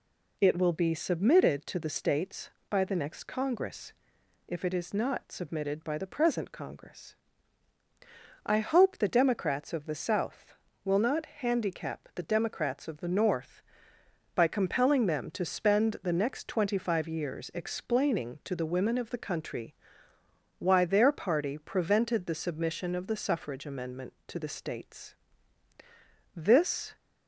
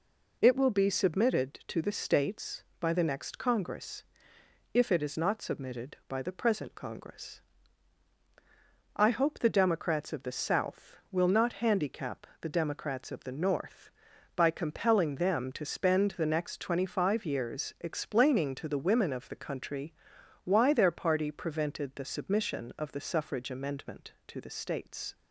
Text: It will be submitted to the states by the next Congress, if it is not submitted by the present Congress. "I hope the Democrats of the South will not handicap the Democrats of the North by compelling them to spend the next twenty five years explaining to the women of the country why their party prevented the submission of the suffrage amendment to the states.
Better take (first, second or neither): second